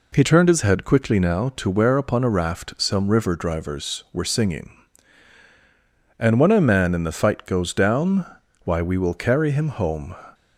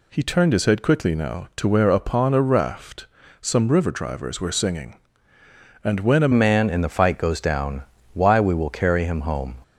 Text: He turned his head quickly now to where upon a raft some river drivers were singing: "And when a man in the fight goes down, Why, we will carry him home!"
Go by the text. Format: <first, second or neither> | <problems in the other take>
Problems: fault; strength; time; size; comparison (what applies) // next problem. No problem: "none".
first | pauses between "raft" and "some"; slight; at 3.0 s; 0.34 s long // changes voice at "man"; from 6.3 s on; 3.2 s long